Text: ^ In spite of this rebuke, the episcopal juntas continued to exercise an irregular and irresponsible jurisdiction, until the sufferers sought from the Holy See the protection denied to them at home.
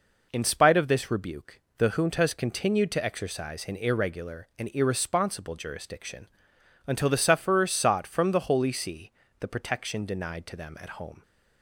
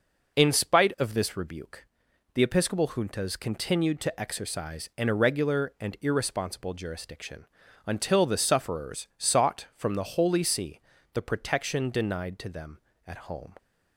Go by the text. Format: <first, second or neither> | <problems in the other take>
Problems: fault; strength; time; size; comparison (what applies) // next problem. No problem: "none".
second | skips "episcopal"; at 1.8 s // pauses between "See" and "the"; slight; at 9.1 s; 0.28 s long; slight in the second